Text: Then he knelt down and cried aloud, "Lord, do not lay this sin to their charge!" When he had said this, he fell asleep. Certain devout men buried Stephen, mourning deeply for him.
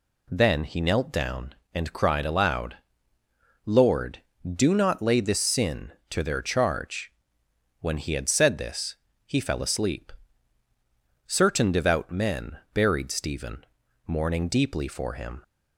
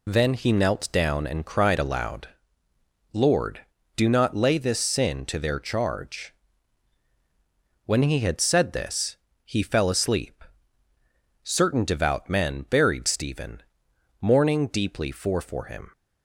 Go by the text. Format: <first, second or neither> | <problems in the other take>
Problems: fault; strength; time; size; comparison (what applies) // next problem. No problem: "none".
first | says "for" twice; at 15.4 s